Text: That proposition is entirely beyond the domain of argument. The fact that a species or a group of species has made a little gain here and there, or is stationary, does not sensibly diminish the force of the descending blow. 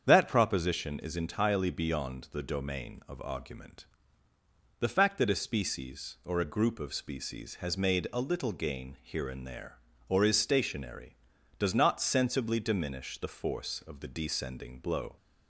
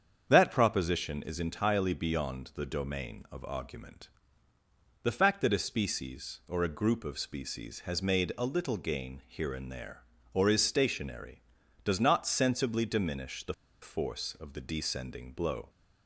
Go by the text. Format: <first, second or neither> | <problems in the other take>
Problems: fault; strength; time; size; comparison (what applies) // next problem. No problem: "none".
first | starts louder than the rest; strong; until 1.3 s; 7.5 dB; strong in the first // pauses between "the" and "force"; slight; at 13.5 s; 0.29 s long